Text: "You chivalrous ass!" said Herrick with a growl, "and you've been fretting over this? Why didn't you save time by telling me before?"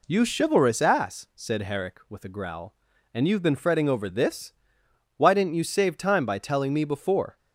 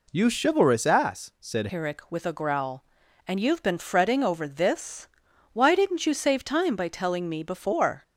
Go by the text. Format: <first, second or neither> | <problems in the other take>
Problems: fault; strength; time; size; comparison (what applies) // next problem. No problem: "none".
first | changes voice at "Herrick"; from 1.7 s on; 6.3 s long